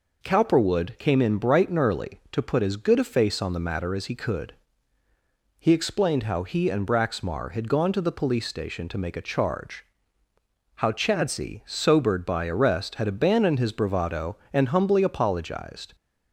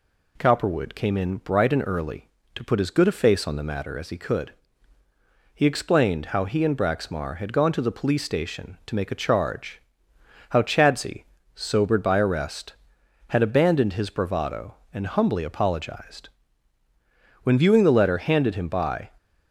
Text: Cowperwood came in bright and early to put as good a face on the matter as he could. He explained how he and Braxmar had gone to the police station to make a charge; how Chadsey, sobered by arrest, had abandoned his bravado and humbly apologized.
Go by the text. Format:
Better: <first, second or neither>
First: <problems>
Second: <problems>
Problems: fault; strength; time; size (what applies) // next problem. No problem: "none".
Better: first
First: none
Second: goes on to say "When viewing the letter handed him by"; strong; from 17.4 s on; 1.6 s long